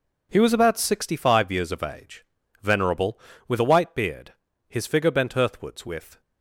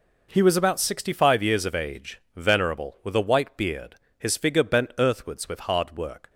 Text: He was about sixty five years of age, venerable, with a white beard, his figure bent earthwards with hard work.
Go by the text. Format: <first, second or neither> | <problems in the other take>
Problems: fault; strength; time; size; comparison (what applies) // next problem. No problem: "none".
second | stops before "hard work"; at 6.2 s